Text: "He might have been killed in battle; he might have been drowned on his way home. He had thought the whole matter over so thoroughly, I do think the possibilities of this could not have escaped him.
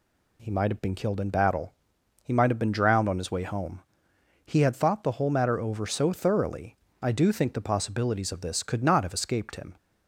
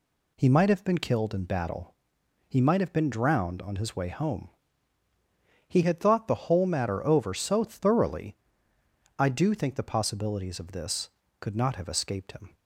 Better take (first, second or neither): neither